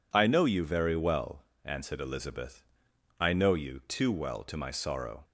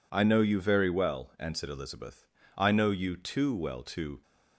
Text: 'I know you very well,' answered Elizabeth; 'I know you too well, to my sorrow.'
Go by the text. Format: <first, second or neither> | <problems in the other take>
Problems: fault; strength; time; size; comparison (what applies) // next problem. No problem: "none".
first | stops before "my sorrow"; at 4.2 s